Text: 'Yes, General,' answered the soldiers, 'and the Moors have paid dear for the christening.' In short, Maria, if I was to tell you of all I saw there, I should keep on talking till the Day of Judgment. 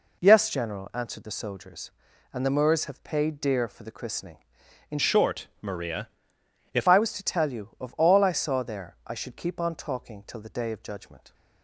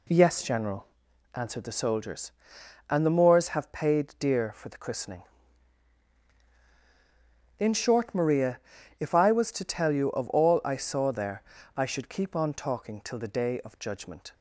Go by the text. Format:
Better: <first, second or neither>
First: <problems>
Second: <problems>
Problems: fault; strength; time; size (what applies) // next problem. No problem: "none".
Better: second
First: changes voice from "short" to "if"; from 4.9 to 6.8 s; 1.9 s long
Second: none